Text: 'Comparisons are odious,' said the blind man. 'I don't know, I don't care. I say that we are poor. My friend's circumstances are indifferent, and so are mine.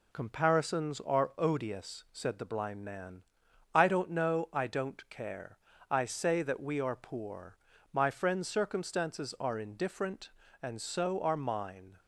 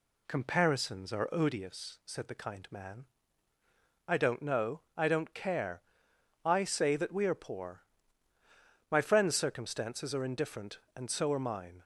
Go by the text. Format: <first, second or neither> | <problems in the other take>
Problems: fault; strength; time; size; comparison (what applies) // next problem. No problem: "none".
first | says "kind" for "blind"; at 2.3 s